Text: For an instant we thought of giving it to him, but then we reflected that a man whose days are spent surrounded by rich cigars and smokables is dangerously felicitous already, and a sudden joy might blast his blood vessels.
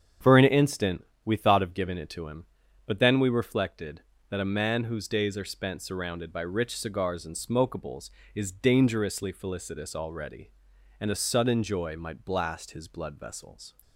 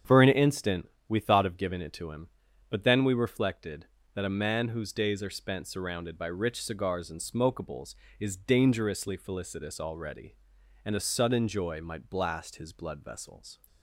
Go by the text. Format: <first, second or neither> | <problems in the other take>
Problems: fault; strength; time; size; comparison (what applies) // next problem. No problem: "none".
neither | starts louder than the rest; strong; the same in both // pauses between "instant" and "we"; slight; the same in both